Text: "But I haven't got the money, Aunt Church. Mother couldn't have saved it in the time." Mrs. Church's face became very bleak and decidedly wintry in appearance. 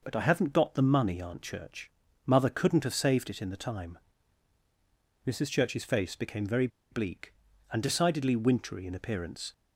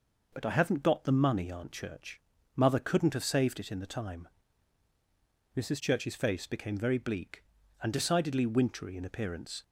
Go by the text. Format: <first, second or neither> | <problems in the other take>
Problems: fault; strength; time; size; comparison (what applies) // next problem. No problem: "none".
second | pauses between "very" and "bleak"; slight; at 6.6 s; 0.23 s long